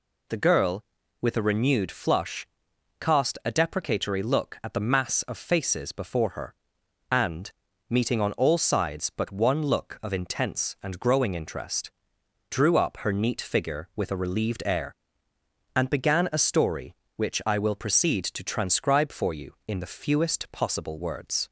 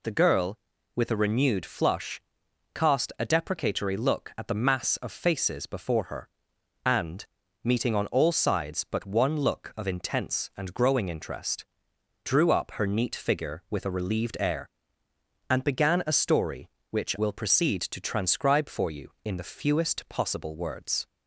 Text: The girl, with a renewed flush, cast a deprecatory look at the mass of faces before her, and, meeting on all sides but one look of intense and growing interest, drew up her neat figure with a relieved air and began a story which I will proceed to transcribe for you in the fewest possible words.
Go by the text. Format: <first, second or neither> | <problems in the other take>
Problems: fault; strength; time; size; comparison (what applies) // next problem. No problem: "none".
first | skips "I"; at 17.1 s